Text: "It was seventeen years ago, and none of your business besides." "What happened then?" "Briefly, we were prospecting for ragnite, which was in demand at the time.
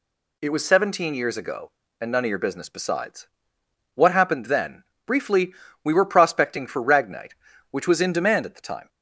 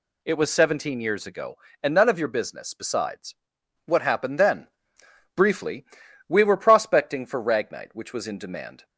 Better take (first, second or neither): first